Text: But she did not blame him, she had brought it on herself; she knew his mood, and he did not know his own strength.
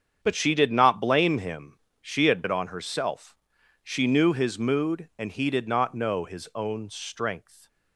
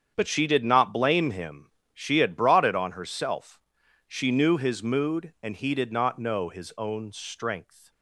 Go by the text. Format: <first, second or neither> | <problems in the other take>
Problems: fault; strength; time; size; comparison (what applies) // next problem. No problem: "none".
second | starts louder than the rest; strong; until 1.2 s; 7.5 dB; strong in the second // skips "brought"; at 2.4 s